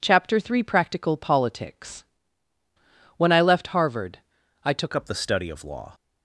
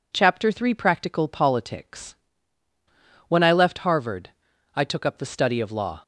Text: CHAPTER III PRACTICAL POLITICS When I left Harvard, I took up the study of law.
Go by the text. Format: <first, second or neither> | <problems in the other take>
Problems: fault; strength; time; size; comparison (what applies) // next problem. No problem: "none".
second | pauses between "POLITICS" and "When"; at 2.0 s; 1.1 s long; also in the second // changes voice at "up"; from 4.9 s on; 1.0 s long